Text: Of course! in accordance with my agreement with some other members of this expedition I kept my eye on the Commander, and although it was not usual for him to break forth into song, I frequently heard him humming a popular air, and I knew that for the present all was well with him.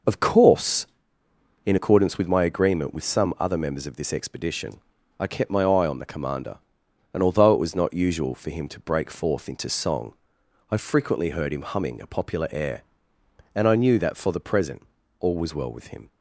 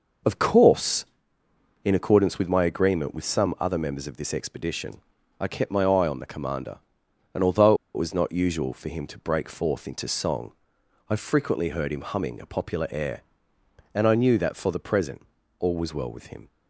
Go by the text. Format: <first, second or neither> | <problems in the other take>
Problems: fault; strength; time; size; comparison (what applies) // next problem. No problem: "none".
first | pauses between "expedition" and "I"; at 5.0 s; 0.40 s long; also in the first // pauses between "although" and "it"; slight; at 7.7 s; 0.19 s long // pauses between "present" and "all"; at 15.2 s; 0.38 s long; also in the first